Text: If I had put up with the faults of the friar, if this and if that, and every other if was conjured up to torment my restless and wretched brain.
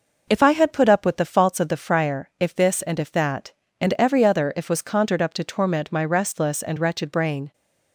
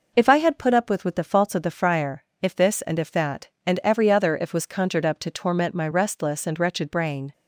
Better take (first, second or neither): first